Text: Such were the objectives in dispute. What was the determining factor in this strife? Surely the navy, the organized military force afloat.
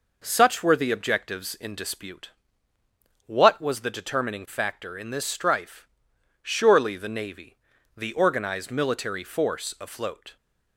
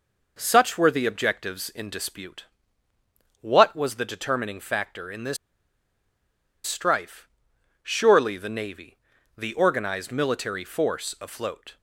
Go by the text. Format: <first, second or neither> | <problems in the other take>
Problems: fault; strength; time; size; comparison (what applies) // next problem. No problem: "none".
first | pauses between "this" and "strife"; strong; at 5.3 s; 1.2 s long